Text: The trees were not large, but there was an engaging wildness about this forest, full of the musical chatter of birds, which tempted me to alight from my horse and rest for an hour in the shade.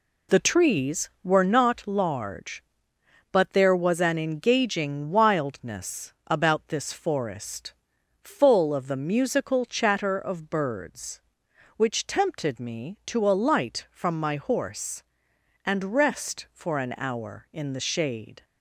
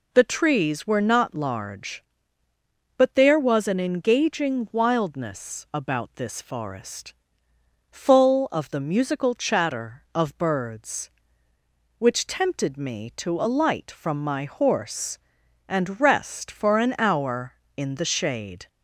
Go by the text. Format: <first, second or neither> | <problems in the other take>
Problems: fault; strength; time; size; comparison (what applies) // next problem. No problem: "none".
neither | none